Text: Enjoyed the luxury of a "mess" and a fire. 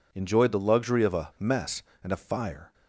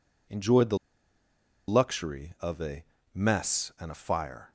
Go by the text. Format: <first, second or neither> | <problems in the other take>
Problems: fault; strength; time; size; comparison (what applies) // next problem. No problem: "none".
first | pauses between "the" and "luxury"; noticeable; at 0.7 s; 0.90 s long // pauses between "a" and "mess"; slight; at 2.8 s; 0.28 s long